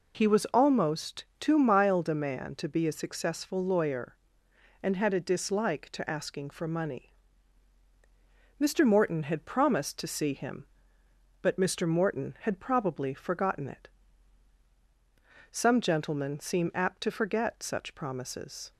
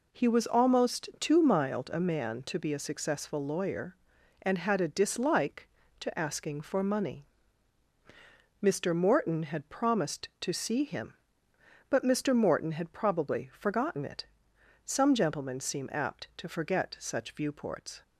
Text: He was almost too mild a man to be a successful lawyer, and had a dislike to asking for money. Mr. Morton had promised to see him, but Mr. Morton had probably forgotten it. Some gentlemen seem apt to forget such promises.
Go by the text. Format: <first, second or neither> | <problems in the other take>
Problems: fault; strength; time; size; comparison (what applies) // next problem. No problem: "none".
first | says "viewports" for "promises"; at 17.3 s